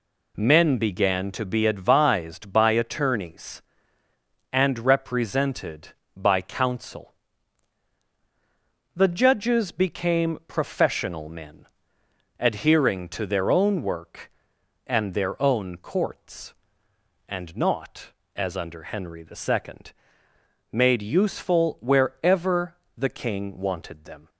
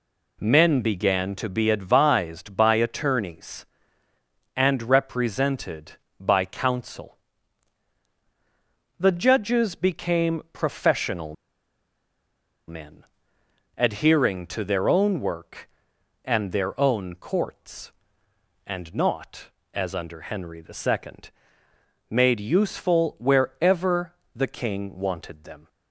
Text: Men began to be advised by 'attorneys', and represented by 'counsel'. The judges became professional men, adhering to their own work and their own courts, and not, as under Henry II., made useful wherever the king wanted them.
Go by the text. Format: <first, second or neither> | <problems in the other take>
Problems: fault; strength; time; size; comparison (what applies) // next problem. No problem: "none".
first | pauses between "professional" and "men"; strong; at 11.3 s; 1.3 s long // pauses between "wherever" and "the"; slight; at 24.1 s; 0.24 s long; slight in the first